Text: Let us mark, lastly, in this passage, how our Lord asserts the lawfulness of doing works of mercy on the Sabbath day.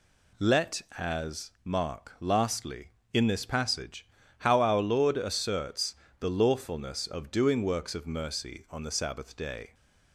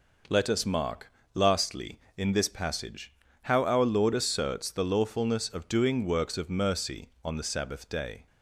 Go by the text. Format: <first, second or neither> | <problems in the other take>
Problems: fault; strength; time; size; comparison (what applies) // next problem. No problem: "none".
second | says "as" for "us"; at 0.9 s // pauses between "asserts" and "the"; slight; at 5.9 s; 0.24 s long